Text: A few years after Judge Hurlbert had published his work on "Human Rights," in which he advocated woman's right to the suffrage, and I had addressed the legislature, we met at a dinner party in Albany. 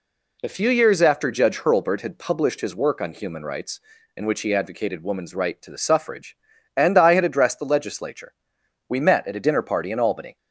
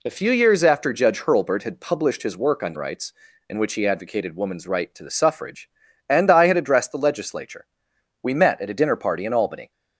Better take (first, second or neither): first